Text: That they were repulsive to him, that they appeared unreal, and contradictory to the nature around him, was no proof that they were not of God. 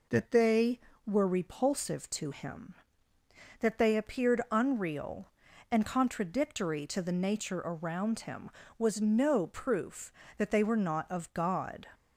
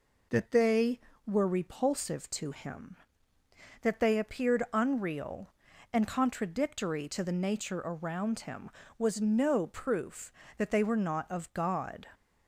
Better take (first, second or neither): neither